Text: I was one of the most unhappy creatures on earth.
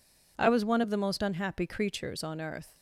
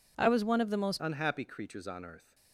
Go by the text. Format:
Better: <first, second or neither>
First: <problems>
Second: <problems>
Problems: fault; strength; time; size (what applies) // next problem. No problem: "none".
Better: first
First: none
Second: changes voice at "unhappy"; from 1.0 s on; 1.3 s long